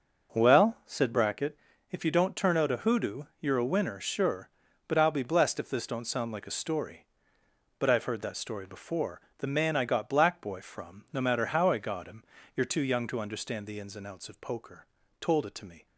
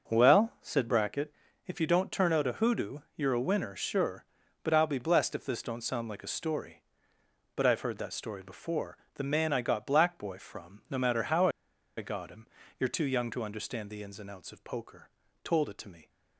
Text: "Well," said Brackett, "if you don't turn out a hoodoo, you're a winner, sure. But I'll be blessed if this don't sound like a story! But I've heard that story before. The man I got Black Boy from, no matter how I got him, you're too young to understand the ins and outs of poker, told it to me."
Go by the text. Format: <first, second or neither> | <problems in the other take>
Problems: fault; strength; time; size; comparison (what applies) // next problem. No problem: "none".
first | pauses between "how" and "I"; noticeable; at 11.4 s; 0.49 s long